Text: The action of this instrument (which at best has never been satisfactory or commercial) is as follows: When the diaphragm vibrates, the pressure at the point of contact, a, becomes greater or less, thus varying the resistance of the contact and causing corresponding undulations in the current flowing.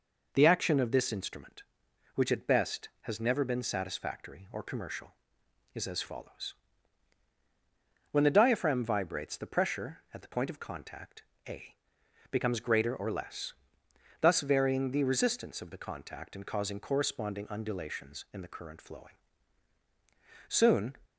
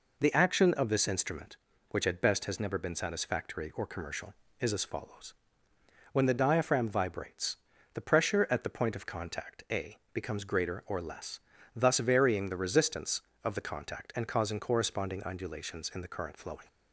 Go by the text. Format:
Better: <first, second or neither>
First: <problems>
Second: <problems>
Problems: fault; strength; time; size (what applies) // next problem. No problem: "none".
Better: second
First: goes on to say "Soon"; slight; from 20.4 s on; 0.48 s long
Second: none